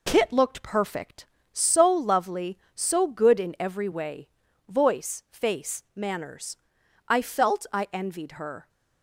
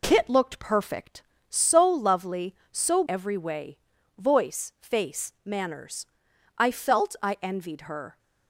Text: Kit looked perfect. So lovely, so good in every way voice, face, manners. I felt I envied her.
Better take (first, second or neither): first